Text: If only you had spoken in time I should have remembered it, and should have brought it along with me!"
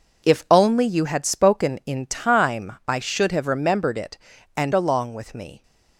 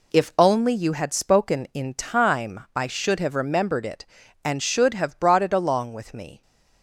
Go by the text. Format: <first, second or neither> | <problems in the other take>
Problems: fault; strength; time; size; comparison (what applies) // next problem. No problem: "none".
second | skips "should have brought it"; at 4.7 s